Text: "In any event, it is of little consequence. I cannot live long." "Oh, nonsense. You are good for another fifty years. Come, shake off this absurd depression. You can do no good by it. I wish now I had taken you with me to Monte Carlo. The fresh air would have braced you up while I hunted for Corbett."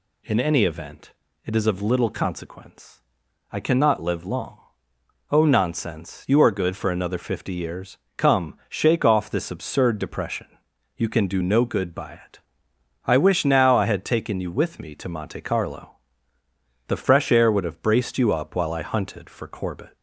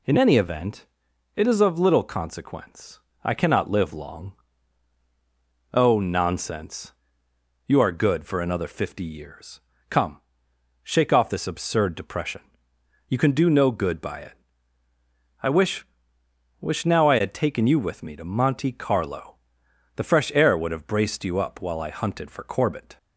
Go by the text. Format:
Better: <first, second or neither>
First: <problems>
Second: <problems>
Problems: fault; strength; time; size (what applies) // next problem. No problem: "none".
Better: first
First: none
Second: says "wish" twice; at 16.6 s